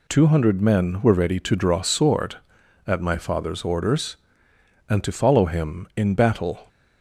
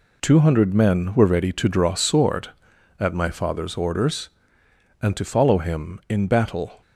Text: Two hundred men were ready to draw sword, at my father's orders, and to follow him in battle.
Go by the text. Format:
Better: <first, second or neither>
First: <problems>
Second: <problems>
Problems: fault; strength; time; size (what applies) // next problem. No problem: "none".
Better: first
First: none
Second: gets quieter; strong; throughout; 9 dB